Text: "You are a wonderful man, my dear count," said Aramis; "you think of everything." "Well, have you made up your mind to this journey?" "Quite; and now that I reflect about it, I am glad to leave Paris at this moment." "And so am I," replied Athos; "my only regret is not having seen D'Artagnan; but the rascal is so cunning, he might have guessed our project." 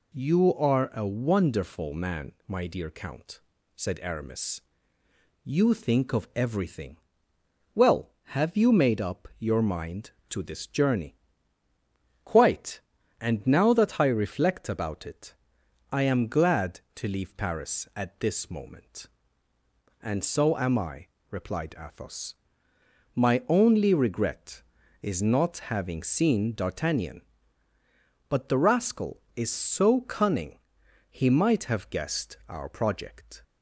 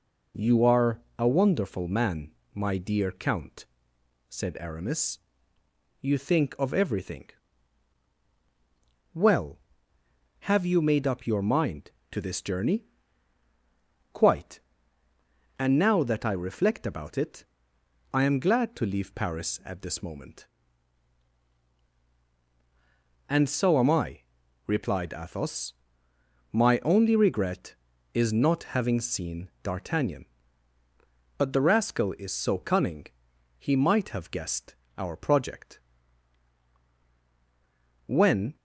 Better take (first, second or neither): first